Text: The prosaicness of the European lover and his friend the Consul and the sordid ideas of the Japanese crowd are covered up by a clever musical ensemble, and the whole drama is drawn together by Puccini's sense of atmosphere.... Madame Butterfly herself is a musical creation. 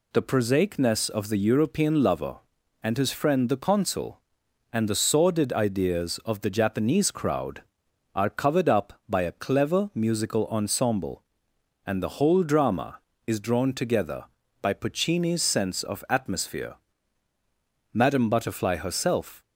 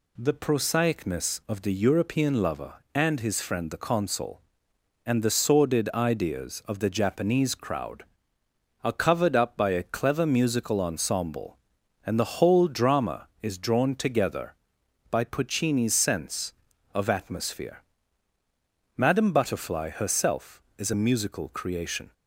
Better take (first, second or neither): second